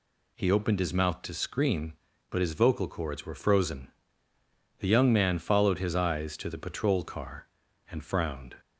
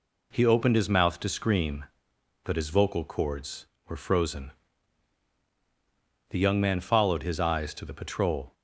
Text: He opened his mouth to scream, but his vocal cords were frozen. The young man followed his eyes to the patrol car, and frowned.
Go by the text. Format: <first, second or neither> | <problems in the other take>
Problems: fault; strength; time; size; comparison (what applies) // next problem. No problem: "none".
first | stops before "car and frowned"; at 8.5 s